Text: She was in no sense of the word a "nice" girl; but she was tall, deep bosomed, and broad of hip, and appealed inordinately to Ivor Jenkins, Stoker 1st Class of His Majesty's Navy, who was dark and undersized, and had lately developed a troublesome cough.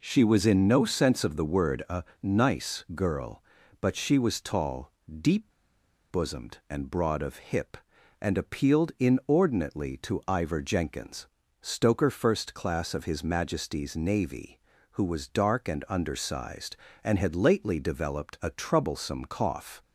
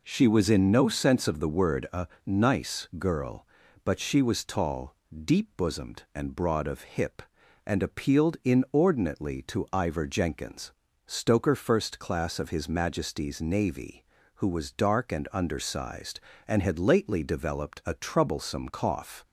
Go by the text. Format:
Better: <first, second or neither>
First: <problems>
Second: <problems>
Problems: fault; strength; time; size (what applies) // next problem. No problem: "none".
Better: second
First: pauses between "a" and "nice"; slight; at 2.0 s; 0.20 s long // pauses between "deep" and "bosomed"; noticeable; at 5.5 s; 0.60 s long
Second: pauses between "a" and "nice"; slight; at 2.0 s; 0.20 s long